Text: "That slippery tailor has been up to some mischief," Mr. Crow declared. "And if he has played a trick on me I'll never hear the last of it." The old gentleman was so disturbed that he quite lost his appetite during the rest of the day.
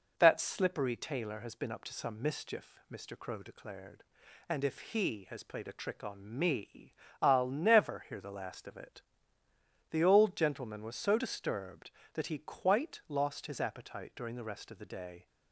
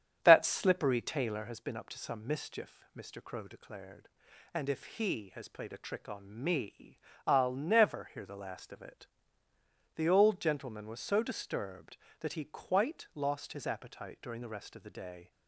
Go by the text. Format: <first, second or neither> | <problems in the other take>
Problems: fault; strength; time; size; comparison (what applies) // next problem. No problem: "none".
first | starts louder than the rest; strong; until 1.6 s; 9 dB // pauses between "me" and "I'll"; slight; at 6.9 s; 0.28 s long; slight in the first